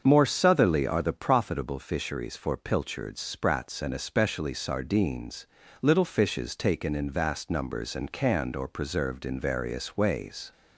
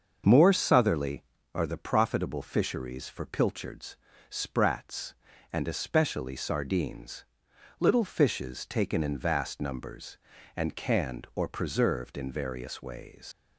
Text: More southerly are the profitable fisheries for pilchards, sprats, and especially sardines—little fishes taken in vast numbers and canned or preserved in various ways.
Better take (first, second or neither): first